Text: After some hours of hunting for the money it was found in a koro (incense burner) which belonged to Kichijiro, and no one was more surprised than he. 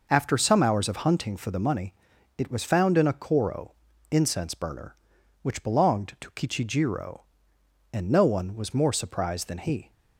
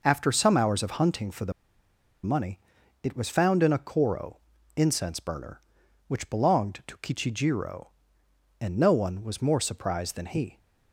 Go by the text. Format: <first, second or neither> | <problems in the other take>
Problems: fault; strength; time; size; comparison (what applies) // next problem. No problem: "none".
first | pauses between "the" and "money"; noticeable; at 1.5 s; 0.72 s long // pauses between "money" and "it"; at 2.5 s; 0.44 s long; also in the first